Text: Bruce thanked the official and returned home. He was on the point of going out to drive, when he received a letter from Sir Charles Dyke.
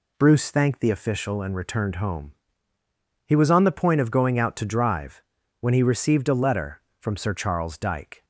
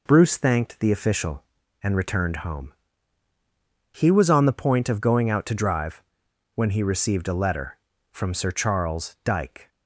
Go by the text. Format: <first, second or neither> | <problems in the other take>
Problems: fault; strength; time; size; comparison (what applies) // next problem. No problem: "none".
neither | none